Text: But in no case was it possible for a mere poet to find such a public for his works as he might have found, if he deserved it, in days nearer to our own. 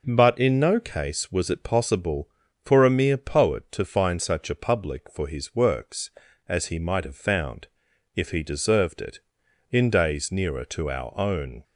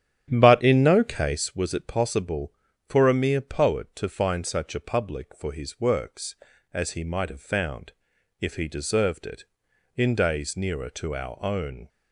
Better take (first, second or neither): first